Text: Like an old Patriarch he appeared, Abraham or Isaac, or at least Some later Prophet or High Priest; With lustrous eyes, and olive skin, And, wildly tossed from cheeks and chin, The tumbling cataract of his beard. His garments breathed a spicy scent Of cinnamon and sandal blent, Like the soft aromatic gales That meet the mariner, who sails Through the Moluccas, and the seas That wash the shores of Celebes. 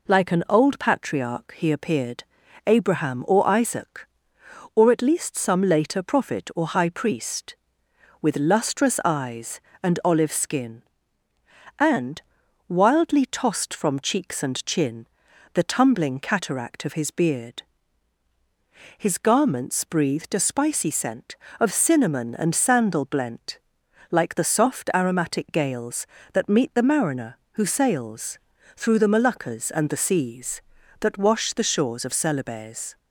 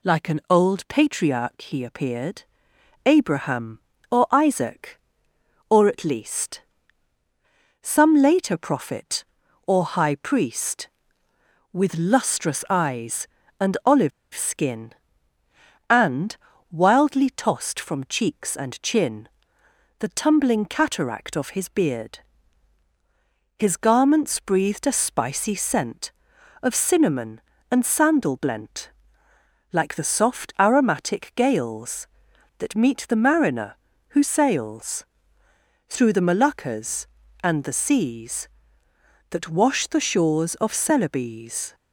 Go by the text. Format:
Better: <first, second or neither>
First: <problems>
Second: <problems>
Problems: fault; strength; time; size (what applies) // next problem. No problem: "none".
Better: first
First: pauses between "sails" and "Through"; at 28.3 s; 0.38 s long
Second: pauses between "least" and "Some"; at 6.6 s; 1.2 s long // pauses between "olive" and "skin"; slight; at 14.1 s; 0.23 s long // pauses between "sails" and "Through"; noticeable; at 35.0 s; 0.82 s long